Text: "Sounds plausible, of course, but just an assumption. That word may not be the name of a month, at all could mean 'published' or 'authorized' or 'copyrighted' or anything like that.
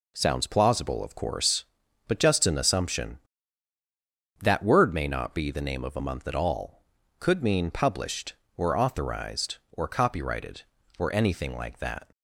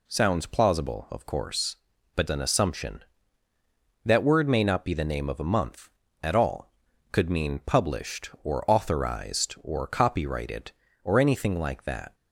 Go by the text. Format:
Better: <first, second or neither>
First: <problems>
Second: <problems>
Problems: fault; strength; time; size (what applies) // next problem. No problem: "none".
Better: first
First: none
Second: skips "just"; at 2.2 s